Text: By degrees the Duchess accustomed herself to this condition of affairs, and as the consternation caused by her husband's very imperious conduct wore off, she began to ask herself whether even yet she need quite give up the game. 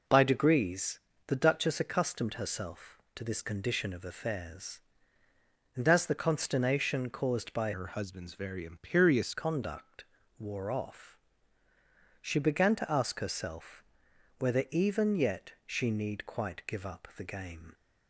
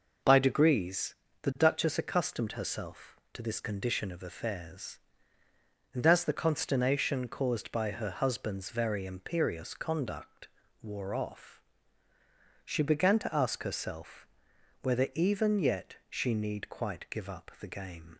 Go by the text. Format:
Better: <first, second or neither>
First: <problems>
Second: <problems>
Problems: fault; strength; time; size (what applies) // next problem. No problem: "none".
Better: second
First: pauses between "degrees" and "the"; slight; at 1.0 s; 0.26 s long // changes voice from "her" to "imperious"; from 7.7 to 9.3 s; 1.6 s long // pauses between "conduct" and "wore"; slight; at 10.0 s; 0.34 s long // pauses between "herself" and "whether"; noticeable; at 13.8 s; 0.54 s long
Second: pauses between "degrees" and "the"; slight; at 1.1 s; 0.26 s long // pauses between "conduct" and "wore"; slight; at 10.4 s; 0.34 s long // pauses between "herself" and "whether"; noticeable; at 14.2 s; 0.54 s long